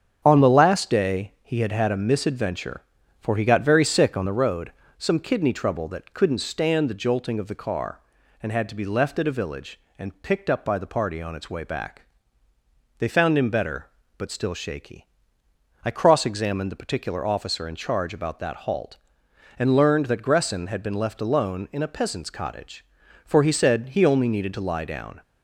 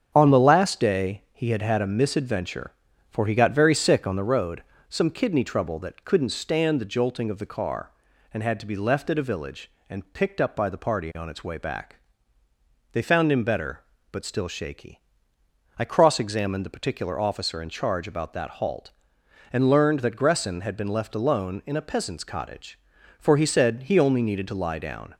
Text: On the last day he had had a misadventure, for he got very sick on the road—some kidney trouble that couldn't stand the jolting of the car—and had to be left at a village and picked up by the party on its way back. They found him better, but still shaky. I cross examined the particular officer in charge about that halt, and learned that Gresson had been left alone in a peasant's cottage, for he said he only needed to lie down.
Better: neither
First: starts louder than the rest; strong; until 1.2 s; 7.5 dB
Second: starts louder than the rest; strong; until 1.1 s; 7.5 dB

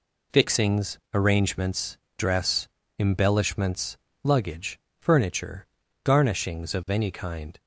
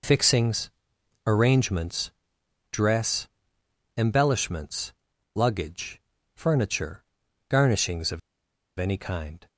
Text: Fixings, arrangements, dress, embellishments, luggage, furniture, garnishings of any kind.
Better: first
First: none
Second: pauses between "of" and "any"; noticeable; at 8.1 s; 0.57 s long

